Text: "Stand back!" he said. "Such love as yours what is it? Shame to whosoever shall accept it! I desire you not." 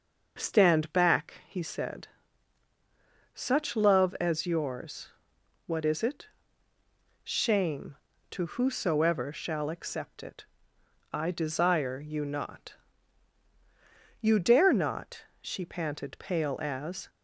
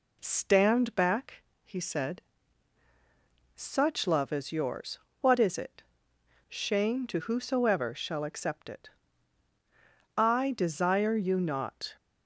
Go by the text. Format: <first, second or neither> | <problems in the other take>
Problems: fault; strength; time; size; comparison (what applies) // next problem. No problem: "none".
second | starts louder than the rest; until 1.3 s; 6 dB // pauses between "yours" and "what"; noticeable; at 5.0 s; 0.56 s long; slight in the second // goes on to say "You dare not she panted pale as"; strong; from 14.2 s on; 2.8 s long